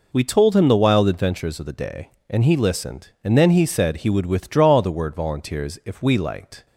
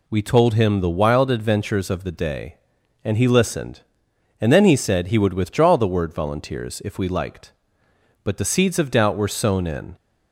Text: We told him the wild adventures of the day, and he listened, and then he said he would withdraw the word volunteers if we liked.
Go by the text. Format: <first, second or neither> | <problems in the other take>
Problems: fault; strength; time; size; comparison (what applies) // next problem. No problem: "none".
first | goes on to say "But the seeds of doubt were sown in"; strong; from 8.2 s on; 1.7 s long